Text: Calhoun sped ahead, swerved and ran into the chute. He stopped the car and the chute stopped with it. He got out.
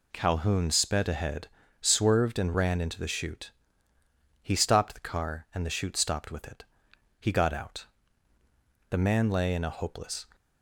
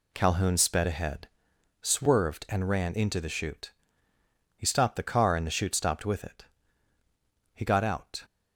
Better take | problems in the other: second | goes on to say "The man lay in a hopeless"; from 8.8 s on; 1.3 s long

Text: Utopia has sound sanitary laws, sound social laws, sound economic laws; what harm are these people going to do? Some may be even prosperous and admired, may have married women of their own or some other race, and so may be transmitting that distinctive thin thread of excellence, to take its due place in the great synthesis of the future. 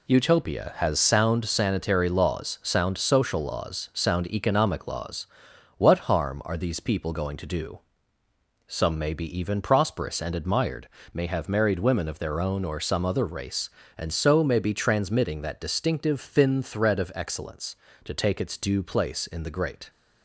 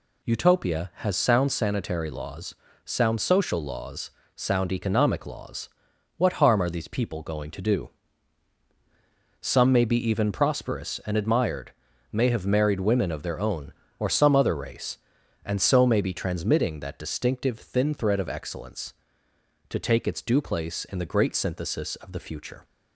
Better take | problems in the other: second | stops before "synthesis of the future"; at 19.8 s

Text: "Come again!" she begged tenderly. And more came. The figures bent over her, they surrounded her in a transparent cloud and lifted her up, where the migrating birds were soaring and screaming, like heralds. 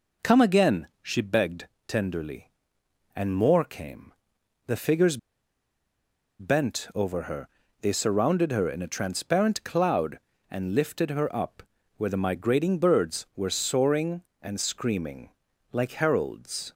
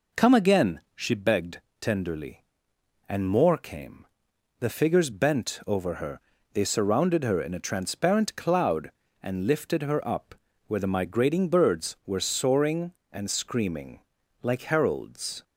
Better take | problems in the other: second | pauses between "begged" and "tenderly"; slight; at 1.6 s; 0.20 s long; slight in the second // pauses between "figures" and "bent"; at 5.1 s; 1.2 s long

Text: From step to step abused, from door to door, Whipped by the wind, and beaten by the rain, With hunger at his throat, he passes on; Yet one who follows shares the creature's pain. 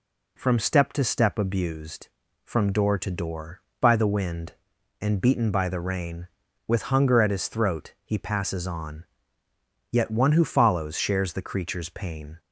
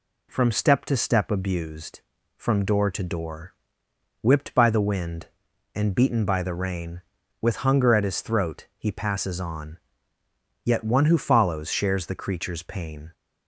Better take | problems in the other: second | skips "Whipped"; at 3.7 s

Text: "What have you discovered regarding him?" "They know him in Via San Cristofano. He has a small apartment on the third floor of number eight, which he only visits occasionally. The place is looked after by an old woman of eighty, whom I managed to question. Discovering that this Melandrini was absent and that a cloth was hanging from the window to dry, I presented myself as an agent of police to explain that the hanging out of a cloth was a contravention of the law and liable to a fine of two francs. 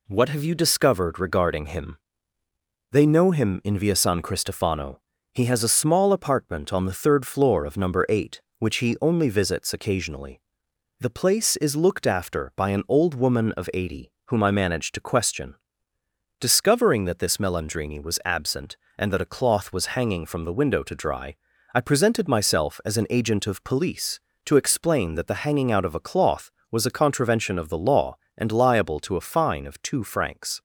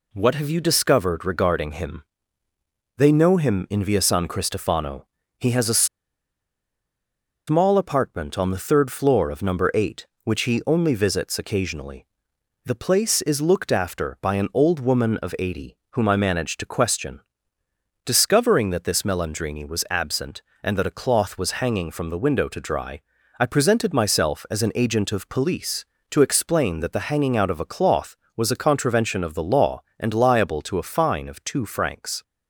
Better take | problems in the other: first | pauses between "a" and "small"; strong; at 5.8 s; 1.6 s long

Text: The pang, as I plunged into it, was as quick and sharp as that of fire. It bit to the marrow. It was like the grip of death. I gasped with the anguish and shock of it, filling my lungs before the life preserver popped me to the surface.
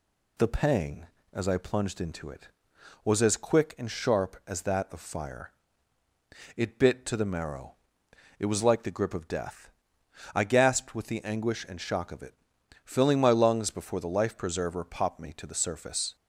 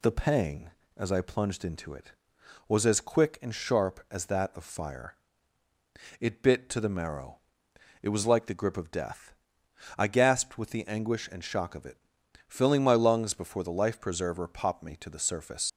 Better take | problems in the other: first | leaves "surface" unfinished; at 15.6 s; 100 ms

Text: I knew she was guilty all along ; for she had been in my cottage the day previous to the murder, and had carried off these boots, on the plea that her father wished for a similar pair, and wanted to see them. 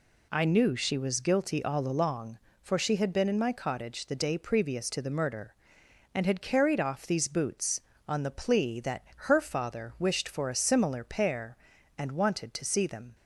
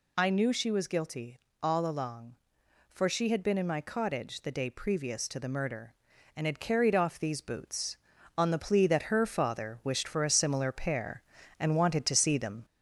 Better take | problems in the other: first | gets louder; slight; throughout; 2.5 dB // pauses between "guilty" and "all"; slight; at 1.3 s; 0.24 s long

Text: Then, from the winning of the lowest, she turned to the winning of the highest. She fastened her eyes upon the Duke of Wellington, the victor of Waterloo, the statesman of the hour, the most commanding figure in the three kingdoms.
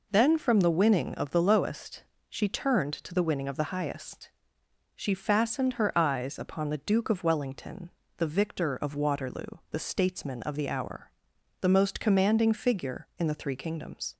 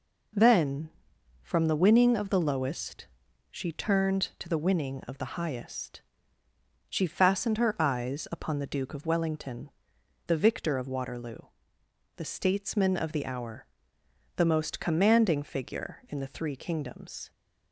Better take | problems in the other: neither | none

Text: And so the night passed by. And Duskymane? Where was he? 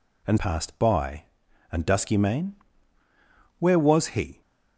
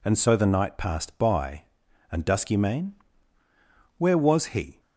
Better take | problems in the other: second | skips "so the night"; at 0.3 s

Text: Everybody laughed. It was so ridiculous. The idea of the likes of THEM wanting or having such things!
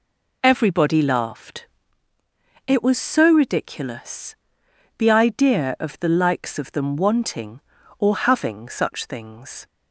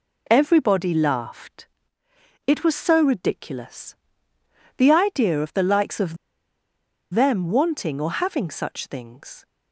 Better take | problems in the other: first | pauses between "of" and "THEM"; noticeable; at 6.1 s; 0.97 s long

